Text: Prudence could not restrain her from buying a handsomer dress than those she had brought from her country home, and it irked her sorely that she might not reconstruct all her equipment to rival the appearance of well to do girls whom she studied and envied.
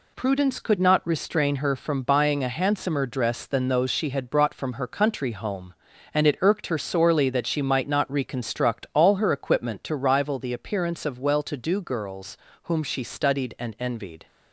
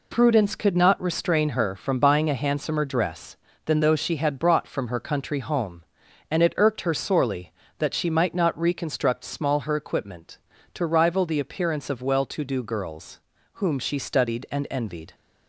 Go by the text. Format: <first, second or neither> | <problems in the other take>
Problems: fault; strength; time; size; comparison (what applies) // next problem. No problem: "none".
first | says "small" for "all"; at 9.2 s // pauses between "girls" and "whom"; slight; at 13.2 s; 0.34 s long; slight in the first